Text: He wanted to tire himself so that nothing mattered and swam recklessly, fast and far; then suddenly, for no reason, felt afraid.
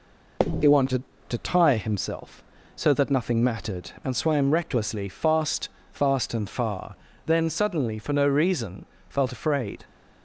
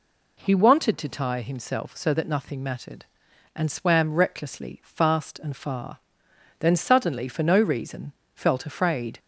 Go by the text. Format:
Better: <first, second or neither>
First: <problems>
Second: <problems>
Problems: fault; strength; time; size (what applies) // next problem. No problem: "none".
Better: second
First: says "fast" twice; at 5.8 s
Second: none